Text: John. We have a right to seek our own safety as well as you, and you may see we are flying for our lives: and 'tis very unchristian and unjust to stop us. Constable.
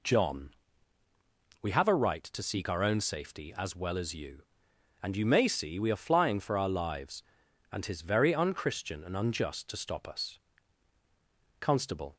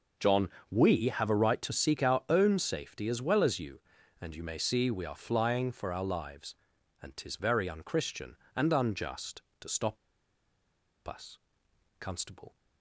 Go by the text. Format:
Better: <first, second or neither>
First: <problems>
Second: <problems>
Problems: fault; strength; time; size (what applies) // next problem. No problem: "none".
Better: first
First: none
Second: pauses between "stop" and "us"; at 9.9 s; 1.1 s long